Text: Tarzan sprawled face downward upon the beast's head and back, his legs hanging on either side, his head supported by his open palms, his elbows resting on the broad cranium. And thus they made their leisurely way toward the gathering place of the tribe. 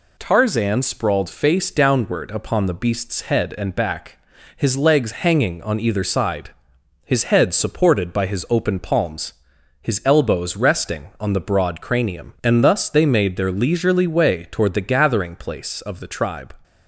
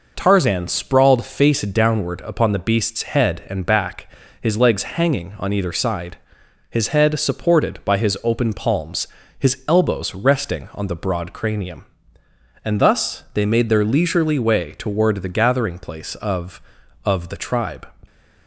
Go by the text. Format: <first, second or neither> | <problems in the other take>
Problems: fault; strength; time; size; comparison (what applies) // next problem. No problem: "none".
first | says "of" twice; at 17.0 s